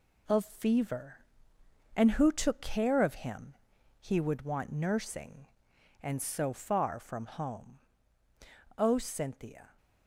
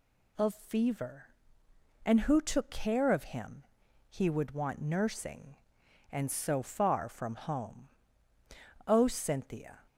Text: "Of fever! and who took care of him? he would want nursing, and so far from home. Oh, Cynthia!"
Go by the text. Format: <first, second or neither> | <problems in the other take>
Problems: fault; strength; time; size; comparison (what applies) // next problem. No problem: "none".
second | gets quieter; noticeable; throughout; 6 dB